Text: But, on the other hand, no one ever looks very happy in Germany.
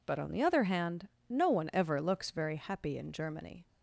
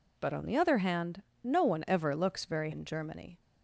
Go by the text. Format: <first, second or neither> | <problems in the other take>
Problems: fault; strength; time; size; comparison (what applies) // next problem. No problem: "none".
first | skips "happy"; at 2.7 s